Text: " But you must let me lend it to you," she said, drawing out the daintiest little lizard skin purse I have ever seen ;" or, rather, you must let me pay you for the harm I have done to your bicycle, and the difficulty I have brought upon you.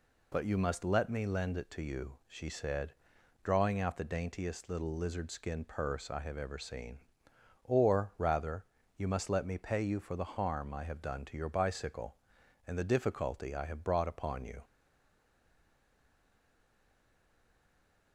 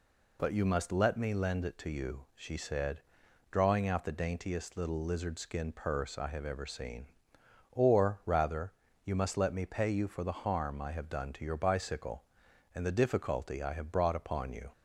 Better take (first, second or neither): second